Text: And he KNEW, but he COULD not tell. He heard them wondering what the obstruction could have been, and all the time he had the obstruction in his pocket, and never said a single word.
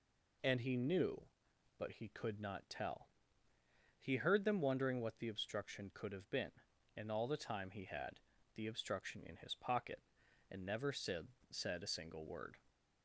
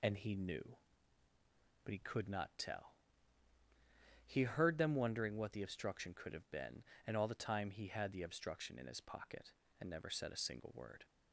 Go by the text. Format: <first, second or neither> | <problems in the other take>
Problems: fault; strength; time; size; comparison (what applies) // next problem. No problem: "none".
second | pauses between "had" and "the"; slight; at 8.1 s; 0.36 s long // says "said" twice; at 11.5 s